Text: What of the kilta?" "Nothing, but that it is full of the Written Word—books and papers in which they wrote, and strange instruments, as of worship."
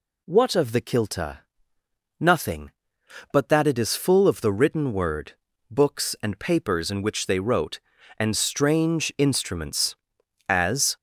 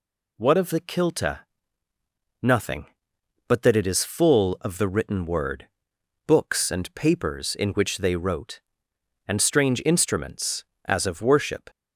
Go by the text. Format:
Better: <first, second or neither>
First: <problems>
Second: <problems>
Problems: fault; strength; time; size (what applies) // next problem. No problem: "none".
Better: second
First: stops before "of worship"; at 10.9 s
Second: none